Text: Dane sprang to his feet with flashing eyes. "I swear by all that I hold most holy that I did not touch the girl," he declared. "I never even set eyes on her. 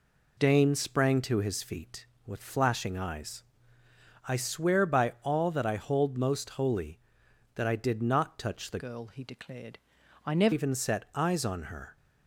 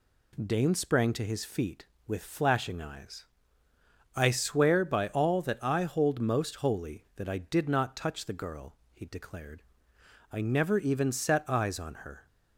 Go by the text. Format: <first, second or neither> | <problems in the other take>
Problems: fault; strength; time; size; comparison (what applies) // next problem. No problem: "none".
second | changes voice from "girl" to "never"; from 8.7 to 10.5 s; 1.8 s long